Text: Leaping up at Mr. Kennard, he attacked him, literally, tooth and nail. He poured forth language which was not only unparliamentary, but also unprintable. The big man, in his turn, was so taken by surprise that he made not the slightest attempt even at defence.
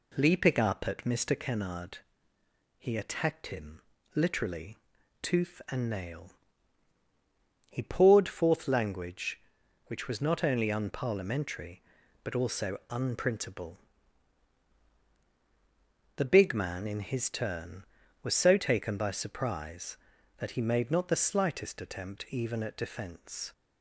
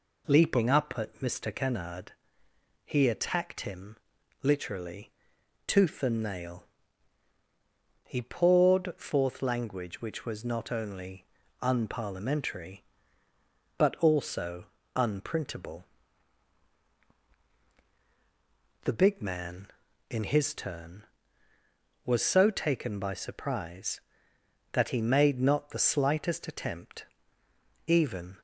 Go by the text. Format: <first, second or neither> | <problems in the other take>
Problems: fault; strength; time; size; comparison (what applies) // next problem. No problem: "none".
first | pauses between "only" and "unparliamentary"; slight; at 11.2 s; 0.35 s long // pauses between "also" and "unprintable"; slight; at 14.6 s; 0.32 s long // pauses between "attempt" and "even"; noticeable; at 27.0 s; 0.82 s long // stops before "at defence"; at 28.3 s